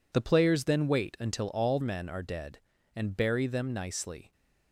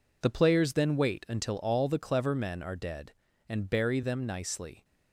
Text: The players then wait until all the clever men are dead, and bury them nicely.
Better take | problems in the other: second | skips "the clever"; at 1.8 s

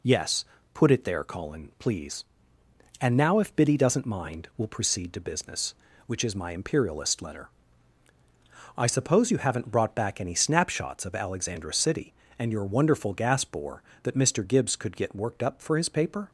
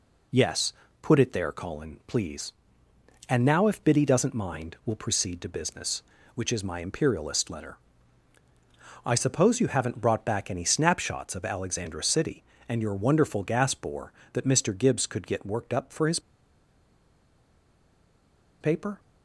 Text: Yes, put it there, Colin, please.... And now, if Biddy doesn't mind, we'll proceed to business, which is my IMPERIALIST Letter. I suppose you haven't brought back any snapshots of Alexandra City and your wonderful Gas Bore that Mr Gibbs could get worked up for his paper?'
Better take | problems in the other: first | pauses between "his" and "paper"; strong; at 16.2 s; 2.3 s long

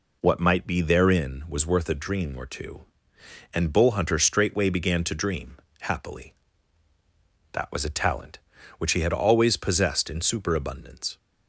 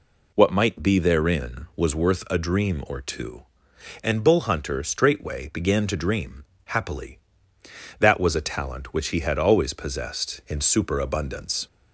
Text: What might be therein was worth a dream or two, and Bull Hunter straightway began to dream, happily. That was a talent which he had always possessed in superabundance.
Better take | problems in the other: neither | none

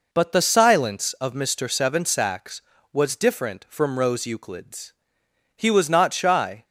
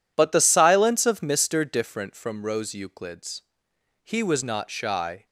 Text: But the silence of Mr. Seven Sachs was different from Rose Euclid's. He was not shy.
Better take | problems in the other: first | skips "Seven Sachs was"; at 1.6 s

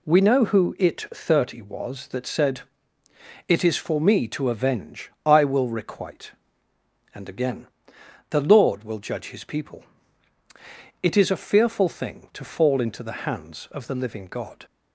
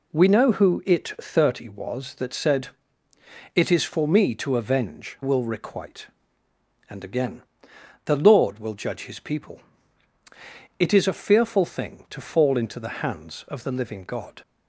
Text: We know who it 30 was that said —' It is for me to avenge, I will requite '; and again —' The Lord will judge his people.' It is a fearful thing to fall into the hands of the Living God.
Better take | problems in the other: first | skips "I"; at 5.2 s

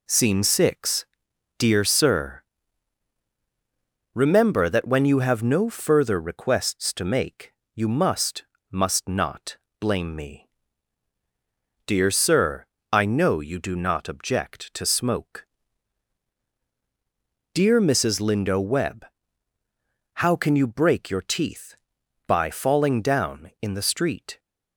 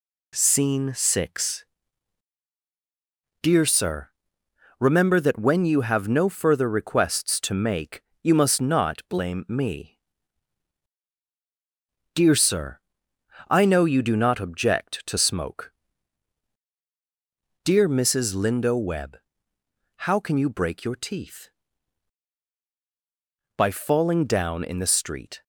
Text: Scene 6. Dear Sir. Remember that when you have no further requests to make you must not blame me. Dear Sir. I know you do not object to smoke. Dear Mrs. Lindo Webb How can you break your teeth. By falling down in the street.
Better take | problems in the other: second | pauses between "make" and "you"; slight; at 7.5 s; 0.22 s long; slight in the second // says "must" twice; at 8.7 s // pauses between "not" and "blame"; slight; at 9.5 s; 0.24 s long // pauses between "Webb" and "How"; at 19.0 s; 1.1 s long; noticeable in the second

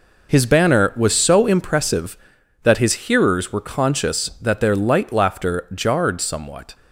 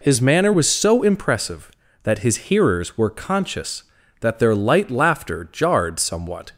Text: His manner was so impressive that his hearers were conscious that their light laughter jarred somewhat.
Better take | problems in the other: second | says "banner" for "manner"; at 0.4 s

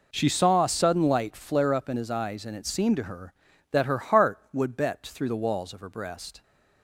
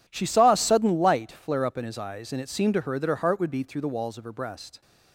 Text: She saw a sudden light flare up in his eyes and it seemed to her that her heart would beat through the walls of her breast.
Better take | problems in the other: second | says "bet" for "beat"; at 4.7 s

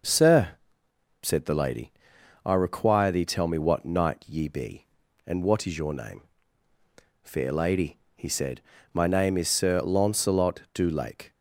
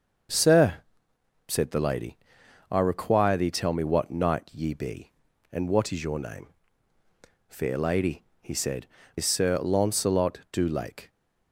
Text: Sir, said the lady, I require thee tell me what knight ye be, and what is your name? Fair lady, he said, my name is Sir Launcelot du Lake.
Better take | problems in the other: first | starts louder than the rest; until 2.0 s; 6 dB // skips "my name"; at 9.0 s

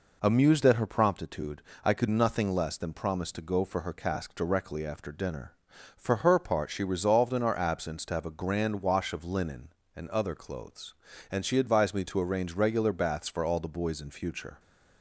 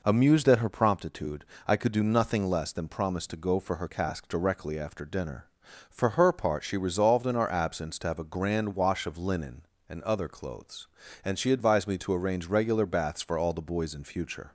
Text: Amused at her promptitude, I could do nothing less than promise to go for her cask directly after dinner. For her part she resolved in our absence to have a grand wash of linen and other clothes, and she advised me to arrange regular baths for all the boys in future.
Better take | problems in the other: second | skips "do"; at 2.0 s

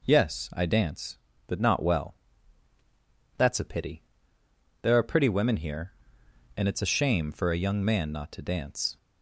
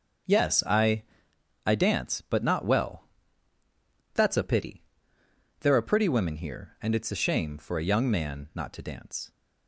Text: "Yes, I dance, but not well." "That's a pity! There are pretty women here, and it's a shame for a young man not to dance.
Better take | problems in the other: first | starts louder than the rest; until 1.9 s; 6.5 dB // says "I" twice; at 1.6 s

